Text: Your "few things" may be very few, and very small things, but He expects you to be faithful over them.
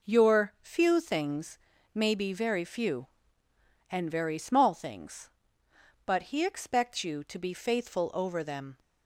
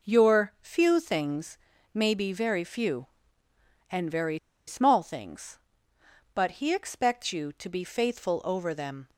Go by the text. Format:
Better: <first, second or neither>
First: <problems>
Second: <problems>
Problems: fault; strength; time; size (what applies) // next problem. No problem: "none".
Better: first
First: pauses between "things" and "may"; slight; at 1.5 s; 0.36 s long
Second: pauses between "things" and "may"; slight; at 1.5 s; 0.36 s long // pauses between "very" and "small"; slight; at 4.3 s; 0.29 s long